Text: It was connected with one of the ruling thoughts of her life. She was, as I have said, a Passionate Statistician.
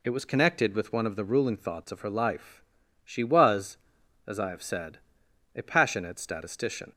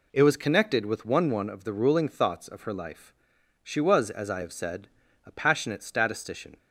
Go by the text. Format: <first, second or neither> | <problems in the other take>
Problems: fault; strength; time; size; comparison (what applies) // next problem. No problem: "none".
first | says "one" twice; at 1.2 s